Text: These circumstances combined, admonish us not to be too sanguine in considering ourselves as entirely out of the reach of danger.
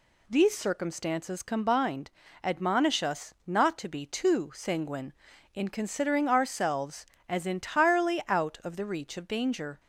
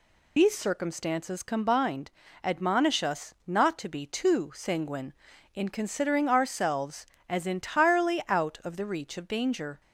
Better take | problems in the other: first | loses the start of "These"; at 0.3 s; 85 ms

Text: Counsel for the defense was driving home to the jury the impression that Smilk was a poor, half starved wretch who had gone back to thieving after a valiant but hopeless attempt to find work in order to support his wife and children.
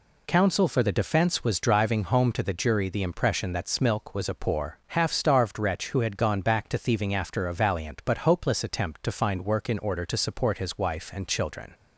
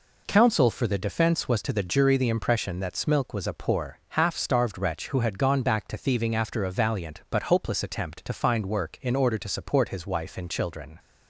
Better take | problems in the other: first | skips "driving home"; at 1.6 s

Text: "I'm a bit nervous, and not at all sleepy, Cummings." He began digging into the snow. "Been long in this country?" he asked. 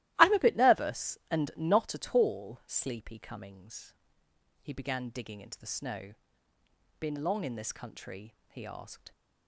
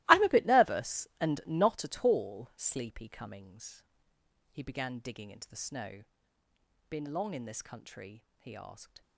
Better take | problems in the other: first | gets quieter; strong; throughout; 15.5 dB // starts louder than the rest; strong; until 1.0 s; 19 dB; strong in the first

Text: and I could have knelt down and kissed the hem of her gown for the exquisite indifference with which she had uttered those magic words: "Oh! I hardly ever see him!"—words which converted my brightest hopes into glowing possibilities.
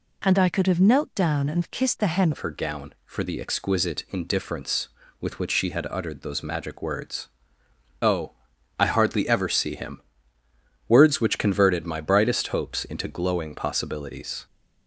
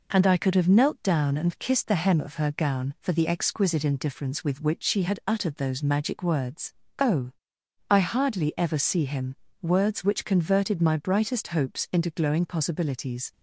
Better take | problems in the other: second | changes voice at "of"; from 2.3 s on; 12.1 s long

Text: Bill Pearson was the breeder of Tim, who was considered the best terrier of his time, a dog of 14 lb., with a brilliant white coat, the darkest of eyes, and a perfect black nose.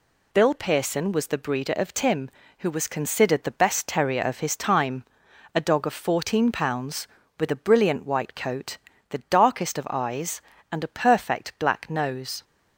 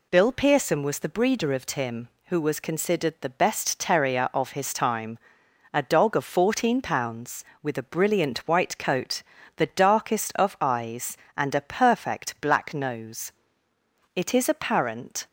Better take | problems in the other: first | goes on to say "It is apparent"; noticeable; from 14.1 s on; 1.1 s long

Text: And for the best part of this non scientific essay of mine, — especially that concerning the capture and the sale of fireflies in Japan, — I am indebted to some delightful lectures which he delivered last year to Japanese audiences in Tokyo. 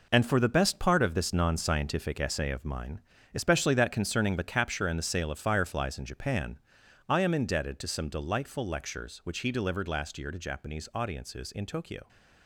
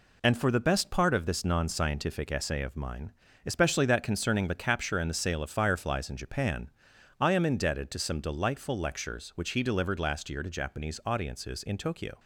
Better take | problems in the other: second | gets quieter; strong; throughout; 9.5 dB

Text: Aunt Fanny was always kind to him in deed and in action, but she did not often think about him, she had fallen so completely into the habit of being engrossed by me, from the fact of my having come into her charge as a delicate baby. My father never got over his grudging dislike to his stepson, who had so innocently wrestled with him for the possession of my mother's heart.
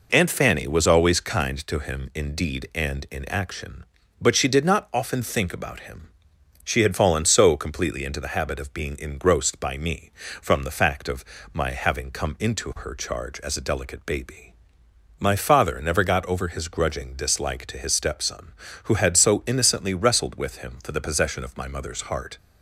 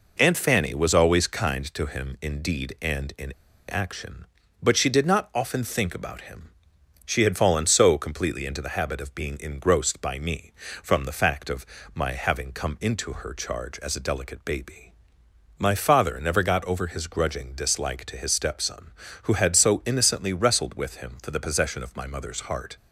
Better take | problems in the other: first | pauses between "in" and "action"; slight; at 3.3 s; 0.35 s long // pauses between "of" and "my"; slight; at 11.6 s; 0.28 s long; slight in the first

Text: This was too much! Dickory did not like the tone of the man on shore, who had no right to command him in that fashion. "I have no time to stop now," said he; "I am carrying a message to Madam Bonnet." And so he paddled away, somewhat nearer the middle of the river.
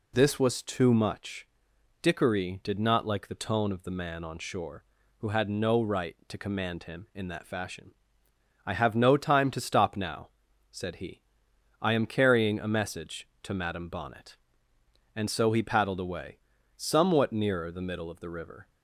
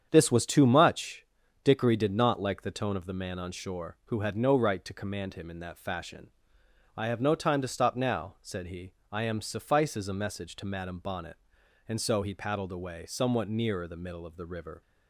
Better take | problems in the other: first | starts louder than the rest; strong; until 1.1 s; 8 dB // says "suffices" for "carrying"; at 9.4 s

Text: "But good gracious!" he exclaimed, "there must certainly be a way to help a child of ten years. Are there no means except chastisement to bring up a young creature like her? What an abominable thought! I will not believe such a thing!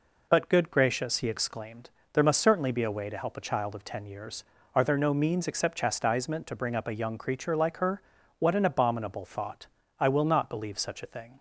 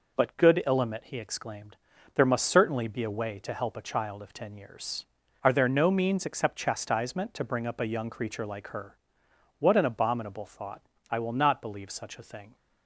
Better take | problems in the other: first | says "illimit" for "gracious"; at 0.6 s

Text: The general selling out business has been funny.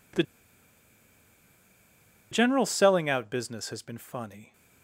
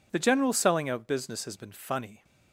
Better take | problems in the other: second | pauses between "The" and "general"; strong; at 0.2 s; 2.0 s long

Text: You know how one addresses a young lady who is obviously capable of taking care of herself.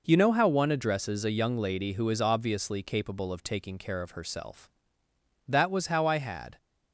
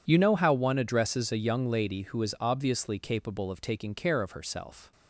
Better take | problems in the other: second | goes on to say "That was how I had"; noticeable; from 5.4 s on; 1.1 s long

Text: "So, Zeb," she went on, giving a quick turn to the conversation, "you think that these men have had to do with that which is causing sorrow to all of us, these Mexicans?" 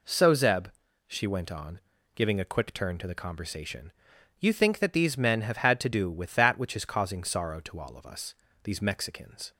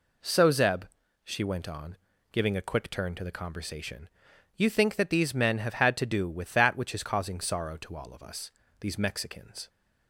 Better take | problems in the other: neither | none

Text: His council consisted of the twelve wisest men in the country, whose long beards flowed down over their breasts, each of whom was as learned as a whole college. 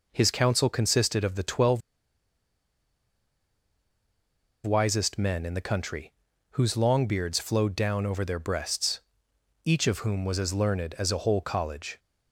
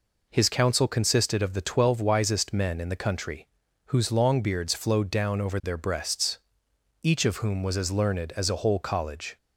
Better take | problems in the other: second | pauses between "twelve" and "wisest"; strong; at 1.8 s; 2.8 s long

